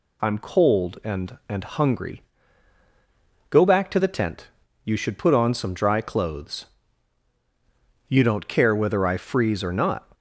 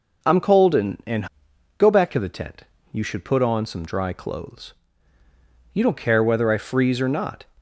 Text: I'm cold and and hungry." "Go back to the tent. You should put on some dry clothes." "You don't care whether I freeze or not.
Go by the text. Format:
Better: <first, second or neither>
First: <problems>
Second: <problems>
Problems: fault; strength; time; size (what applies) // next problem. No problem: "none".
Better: first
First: none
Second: skips "hungry"; at 1.5 s